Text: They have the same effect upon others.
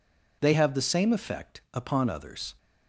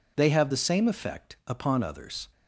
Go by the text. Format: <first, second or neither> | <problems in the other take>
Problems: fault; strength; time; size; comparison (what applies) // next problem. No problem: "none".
neither | none